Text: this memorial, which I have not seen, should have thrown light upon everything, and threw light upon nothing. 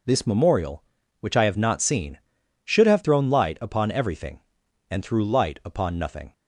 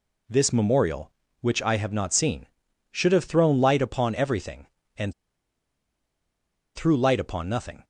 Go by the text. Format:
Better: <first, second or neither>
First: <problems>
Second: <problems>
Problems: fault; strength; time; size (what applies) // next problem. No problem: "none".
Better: first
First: none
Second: pauses between "and" and "threw"; strong; at 5.1 s; 1.6 s long